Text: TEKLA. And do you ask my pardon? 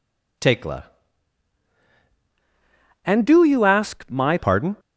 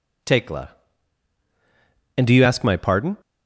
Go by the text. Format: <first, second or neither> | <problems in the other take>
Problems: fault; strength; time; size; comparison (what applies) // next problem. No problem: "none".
second | changes voice from "And" to "my"; from 3.0 to 4.3 s; 1.3 s long